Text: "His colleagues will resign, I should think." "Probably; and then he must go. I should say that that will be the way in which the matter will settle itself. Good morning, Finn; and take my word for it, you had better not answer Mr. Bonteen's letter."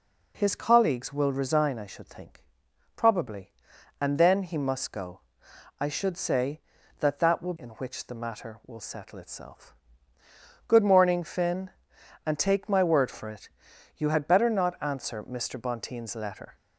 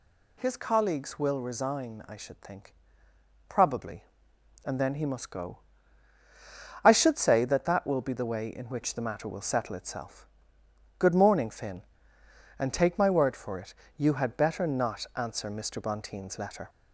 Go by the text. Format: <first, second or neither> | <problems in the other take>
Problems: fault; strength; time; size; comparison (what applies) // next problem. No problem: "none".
second | skips "be the way"; at 7.5 s